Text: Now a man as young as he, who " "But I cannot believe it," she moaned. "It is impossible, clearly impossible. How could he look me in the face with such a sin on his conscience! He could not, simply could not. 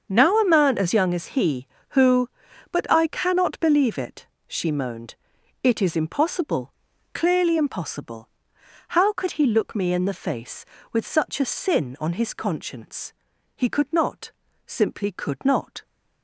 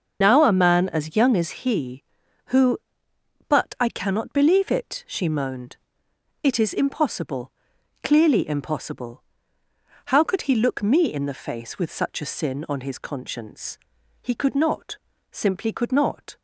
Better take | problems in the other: first | loses the start of "Now"; at 0.2 s; 90 ms // starts louder than the rest; noticeable; until 1.2 s; 6 dB; also in the first

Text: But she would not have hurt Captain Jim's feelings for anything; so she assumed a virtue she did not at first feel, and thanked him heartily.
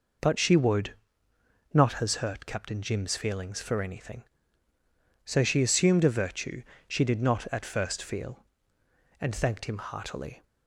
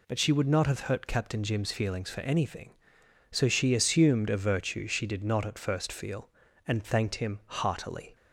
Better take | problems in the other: second | pauses between "would" and "not"; noticeable; at 0.9 s; 0.78 s long // says "has" for "have"; at 1.9 s // pauses between "virtue" and "she"; slight; at 6.6 s; 0.28 s long

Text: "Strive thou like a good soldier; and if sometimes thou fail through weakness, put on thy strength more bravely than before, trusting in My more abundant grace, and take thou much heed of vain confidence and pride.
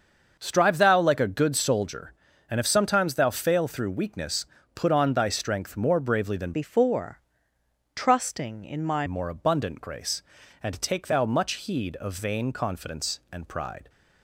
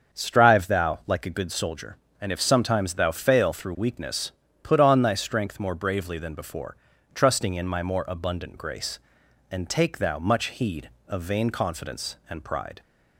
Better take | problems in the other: second | starts louder than the rest; until 1.4 s; 6.5 dB; also in the second // changes voice from "before" to "My"; from 6.5 to 9.0 s; 2.5 s long

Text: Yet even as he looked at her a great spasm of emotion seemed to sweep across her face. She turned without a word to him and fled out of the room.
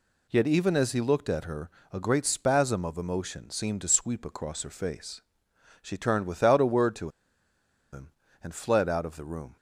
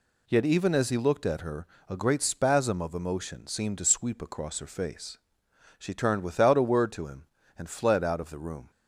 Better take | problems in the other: second | pauses between "her" and "a"; slight; at 1.7 s; 0.20 s long; slight in the second // pauses between "to" and "him"; noticeable; at 7.0 s; 0.84 s long

